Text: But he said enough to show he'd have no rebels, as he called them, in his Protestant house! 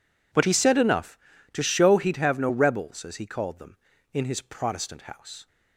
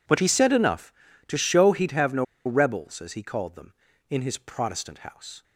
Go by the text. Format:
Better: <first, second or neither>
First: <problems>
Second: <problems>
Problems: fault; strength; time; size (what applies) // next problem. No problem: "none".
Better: first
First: none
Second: pauses between "no" and "rebels"; slight; at 2.2 s; 0.20 s long